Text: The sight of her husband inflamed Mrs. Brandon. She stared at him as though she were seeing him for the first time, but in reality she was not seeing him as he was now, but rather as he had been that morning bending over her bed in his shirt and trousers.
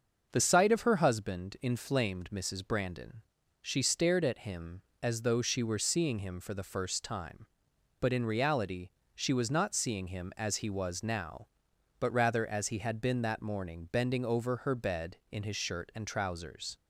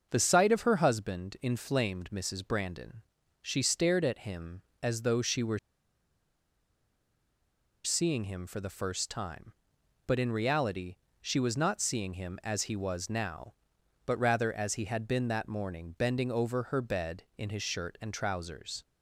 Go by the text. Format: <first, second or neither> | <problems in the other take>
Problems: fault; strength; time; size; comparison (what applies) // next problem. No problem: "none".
first | starts louder than the rest; until 1.1 s; 6.5 dB; also in the first // pauses between "were" and "seeing"; strong; at 5.5 s; 2.2 s long // pauses between "reality" and "she"; slight; at 10.9 s; 0.24 s long; slight in the first